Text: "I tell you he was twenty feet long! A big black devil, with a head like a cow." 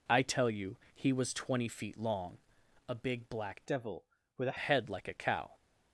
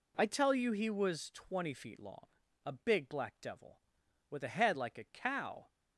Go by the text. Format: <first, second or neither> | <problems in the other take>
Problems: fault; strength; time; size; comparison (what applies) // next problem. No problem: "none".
second | pauses between "you" and "he"; slight; at 0.7 s; 0.18 s long // changes voice from "devil" to "a"; from 3.6 to 4.5 s; 0.9 s long